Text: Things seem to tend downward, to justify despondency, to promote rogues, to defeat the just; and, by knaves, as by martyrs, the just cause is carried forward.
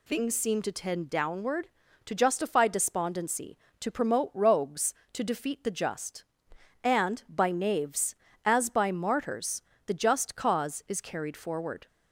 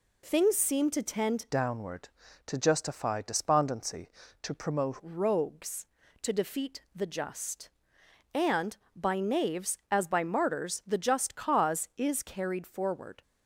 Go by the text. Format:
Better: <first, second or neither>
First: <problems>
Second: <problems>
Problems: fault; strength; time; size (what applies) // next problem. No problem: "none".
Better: first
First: none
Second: changes voice from "downward" to "promote"; from 1.4 to 4.9 s; 3.5 s long